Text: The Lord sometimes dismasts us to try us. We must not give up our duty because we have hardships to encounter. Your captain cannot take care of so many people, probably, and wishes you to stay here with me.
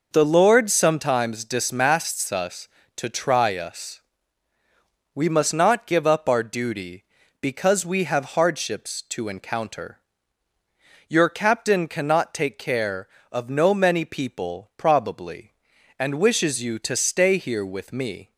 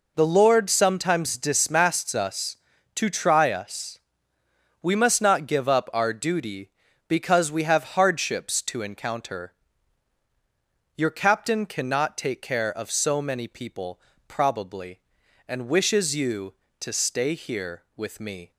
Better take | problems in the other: second | says "no" for "so"; at 13.4 s

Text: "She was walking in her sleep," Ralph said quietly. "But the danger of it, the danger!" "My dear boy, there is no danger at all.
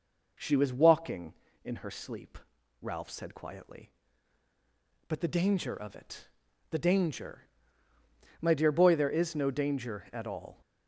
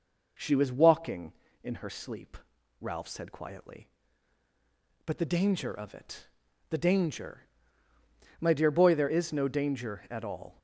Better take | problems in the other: neither | none

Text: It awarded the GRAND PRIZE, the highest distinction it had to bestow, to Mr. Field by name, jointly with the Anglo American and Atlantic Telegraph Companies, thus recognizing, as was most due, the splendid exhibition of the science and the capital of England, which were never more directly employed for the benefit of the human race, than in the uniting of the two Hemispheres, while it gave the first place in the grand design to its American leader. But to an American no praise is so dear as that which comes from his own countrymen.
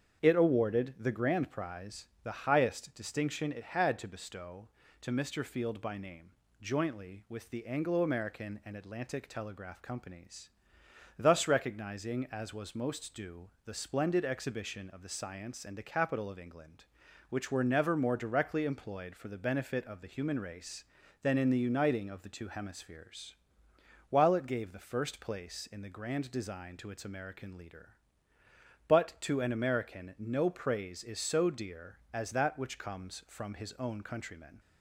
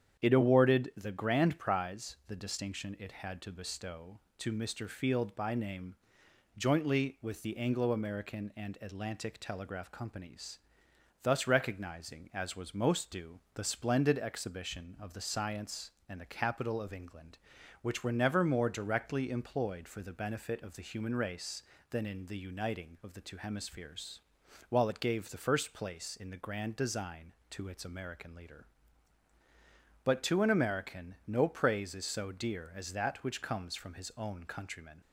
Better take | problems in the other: first | starts louder than the rest; strong; until 1.2 s; 8.5 dB; strong in the first // skips "highest"; at 2.3 s

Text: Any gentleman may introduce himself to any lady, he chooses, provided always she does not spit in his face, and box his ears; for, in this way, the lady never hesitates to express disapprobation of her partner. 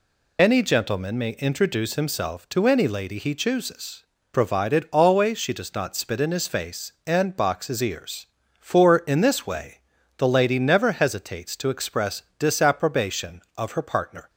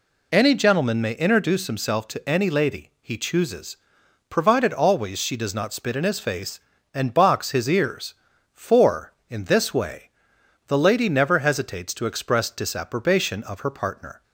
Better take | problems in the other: second | loses the start of "Any"; at 0.3 s; 50 ms // pauses between "express" and "disapprobation"; slight; at 12.2 s; 0.16 s long

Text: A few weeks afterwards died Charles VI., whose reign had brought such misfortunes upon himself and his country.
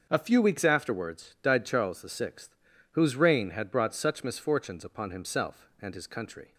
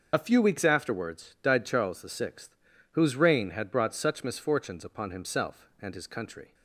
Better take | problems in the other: first | loses the start of "A"; at 0.1 s; 40 ms // starts louder than the rest; until 1.1 s; 6.5 dB; also in the first

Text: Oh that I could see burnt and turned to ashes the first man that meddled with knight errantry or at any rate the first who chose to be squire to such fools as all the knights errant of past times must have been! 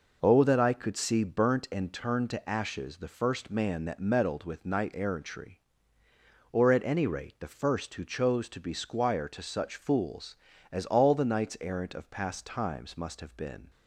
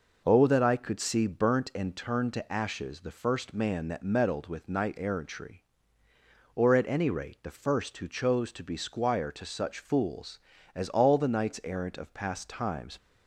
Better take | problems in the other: first | stops before "must have been"; at 12.9 s

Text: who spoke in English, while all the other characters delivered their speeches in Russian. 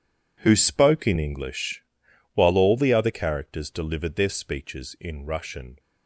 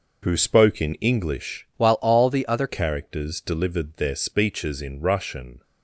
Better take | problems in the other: first | changes voice from "while" to "other"; from 1.7 to 2.6 s; 0.9 s long

